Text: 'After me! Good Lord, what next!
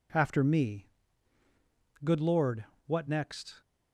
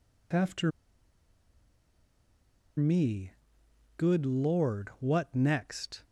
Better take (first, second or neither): first